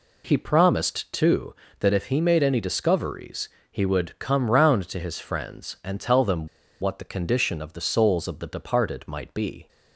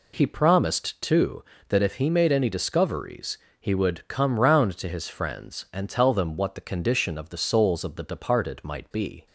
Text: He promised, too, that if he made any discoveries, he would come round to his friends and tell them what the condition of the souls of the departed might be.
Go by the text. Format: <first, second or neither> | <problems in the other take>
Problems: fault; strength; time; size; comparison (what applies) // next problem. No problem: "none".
second | pauses between "them" and "what"; slight; at 6.4 s; 0.33 s long